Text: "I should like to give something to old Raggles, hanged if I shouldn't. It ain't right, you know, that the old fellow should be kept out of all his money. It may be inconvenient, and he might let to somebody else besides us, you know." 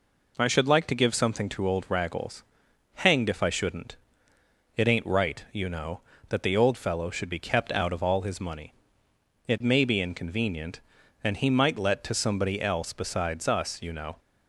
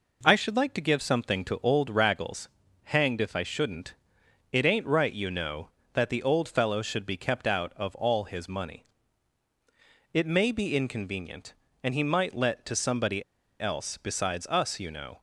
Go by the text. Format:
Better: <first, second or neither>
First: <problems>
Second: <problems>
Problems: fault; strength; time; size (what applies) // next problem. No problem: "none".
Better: first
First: none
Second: pauses between "somebody" and "else"; at 13.2 s; 0.36 s long